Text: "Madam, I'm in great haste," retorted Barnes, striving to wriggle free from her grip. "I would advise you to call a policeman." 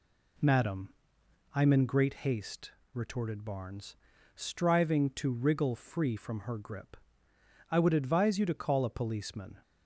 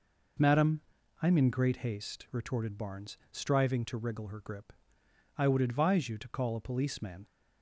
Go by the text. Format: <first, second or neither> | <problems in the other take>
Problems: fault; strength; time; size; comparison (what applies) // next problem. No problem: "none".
first | skips "free from"; at 4.2 s